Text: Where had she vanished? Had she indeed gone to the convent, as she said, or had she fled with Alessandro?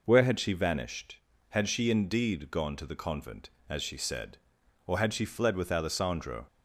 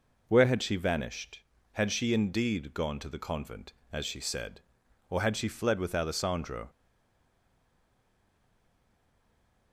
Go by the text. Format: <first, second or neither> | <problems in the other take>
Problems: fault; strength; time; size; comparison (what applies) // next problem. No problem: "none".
first | stays silent after the last word; strong; from 6.6 s on; 3.1 s long